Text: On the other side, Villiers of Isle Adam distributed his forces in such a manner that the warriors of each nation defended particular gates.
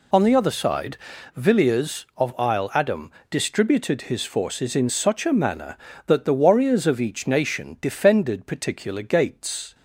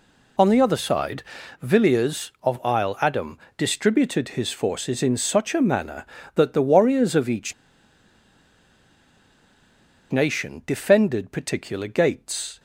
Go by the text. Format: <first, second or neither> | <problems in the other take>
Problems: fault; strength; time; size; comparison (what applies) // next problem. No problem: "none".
first | pauses between "Adam" and "distributed"; slight; at 3.3 s; 0.22 s long; slight in the first // pauses between "each" and "nation"; strong; at 7.5 s; 2.5 s long